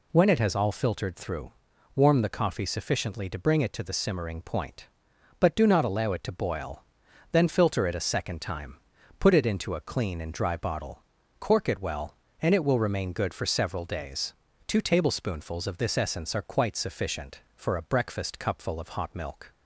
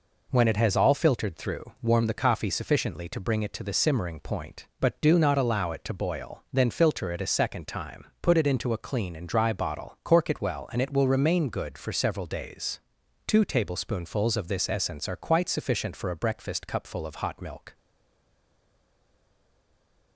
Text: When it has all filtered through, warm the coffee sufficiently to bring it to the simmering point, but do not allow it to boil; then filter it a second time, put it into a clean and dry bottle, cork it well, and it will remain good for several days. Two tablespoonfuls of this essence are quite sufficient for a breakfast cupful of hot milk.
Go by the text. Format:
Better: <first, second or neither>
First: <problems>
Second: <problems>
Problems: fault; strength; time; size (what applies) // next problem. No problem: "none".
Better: first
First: none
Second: stays silent after the last word; from 17.7 s on; 2.4 s long